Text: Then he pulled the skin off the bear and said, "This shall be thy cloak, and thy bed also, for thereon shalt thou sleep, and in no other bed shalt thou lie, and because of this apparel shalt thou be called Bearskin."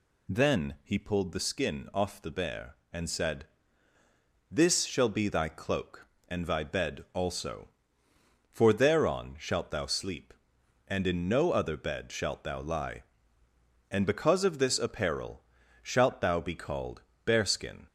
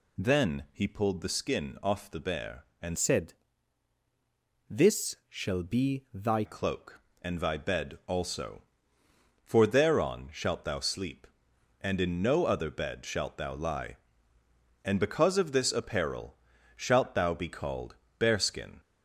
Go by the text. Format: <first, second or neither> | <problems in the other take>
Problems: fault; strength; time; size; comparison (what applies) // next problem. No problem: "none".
first | changes voice from "said" to "thy"; from 2.9 to 6.4 s; 3.5 s long // pauses between "apparel" and "shalt"; at 16.3 s; 0.38 s long; also in the first // pauses between "called" and "Bearskin"; slight; at 17.9 s; 0.24 s long; slight in the first